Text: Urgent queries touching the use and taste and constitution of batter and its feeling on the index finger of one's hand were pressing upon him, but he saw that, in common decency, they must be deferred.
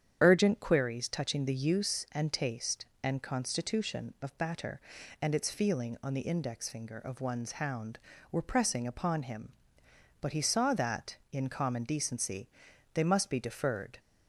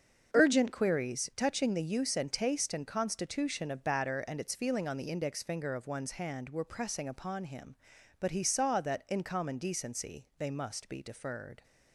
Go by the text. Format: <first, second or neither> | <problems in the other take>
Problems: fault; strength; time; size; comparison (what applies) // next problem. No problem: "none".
second | starts louder than the rest; strong; until 1.2 s; 8.5 dB; also in the second // says "hound" for "hand"; at 7.5 s